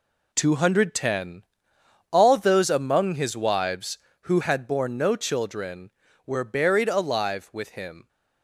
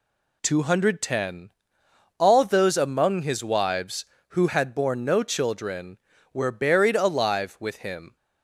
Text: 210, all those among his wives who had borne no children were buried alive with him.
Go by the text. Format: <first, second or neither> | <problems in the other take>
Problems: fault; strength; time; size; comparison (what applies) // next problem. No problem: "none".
second | gets quieter; strong; throughout; 8.5 dB